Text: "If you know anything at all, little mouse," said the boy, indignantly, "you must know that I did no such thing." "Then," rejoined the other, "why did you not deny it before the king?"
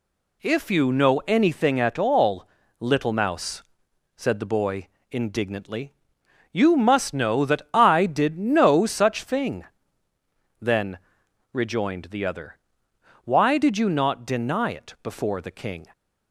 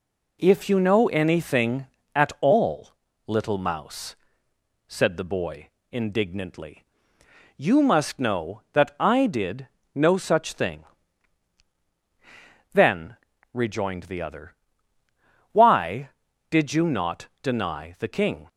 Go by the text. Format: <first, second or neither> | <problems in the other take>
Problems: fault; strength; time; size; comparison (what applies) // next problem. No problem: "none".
first | pauses between "did" and "no"; slight; at 9.6 s; 0.26 s long // skips "it before"; at 17.9 s